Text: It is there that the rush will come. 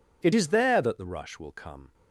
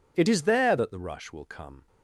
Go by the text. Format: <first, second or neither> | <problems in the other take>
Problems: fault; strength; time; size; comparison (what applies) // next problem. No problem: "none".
neither | none